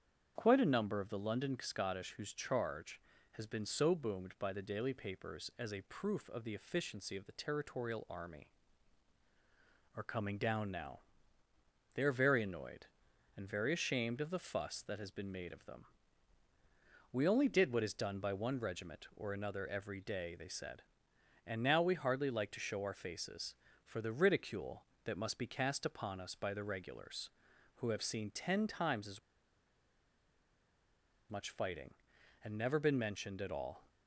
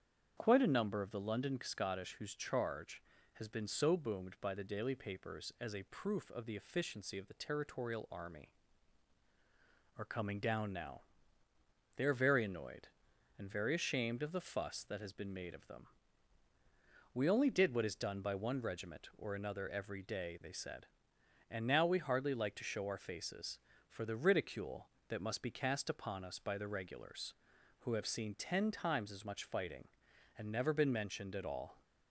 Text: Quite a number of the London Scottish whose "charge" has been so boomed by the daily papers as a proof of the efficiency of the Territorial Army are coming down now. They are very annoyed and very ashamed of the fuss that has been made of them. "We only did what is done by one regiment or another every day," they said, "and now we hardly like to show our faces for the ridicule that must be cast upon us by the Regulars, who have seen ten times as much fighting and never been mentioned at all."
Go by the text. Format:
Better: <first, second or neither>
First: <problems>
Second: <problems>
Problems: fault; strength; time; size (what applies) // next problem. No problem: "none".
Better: second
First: starts louder than the rest; strong; until 1.3 s; 8 dB // pauses between "as" and "much"; strong; at 29.1 s; 2.1 s long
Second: starts louder than the rest; strong; until 1.3 s; 8 dB